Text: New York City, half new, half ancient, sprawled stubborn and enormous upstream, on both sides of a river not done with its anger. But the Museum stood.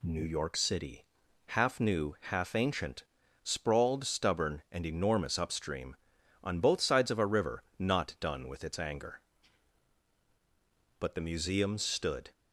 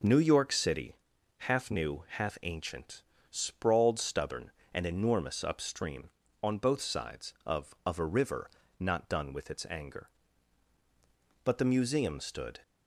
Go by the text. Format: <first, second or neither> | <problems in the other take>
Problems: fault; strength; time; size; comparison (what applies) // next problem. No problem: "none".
first | says "of" twice; at 7.8 s // pauses between "river" and "not"; slight; at 8.5 s; 0.30 s long; slight in the first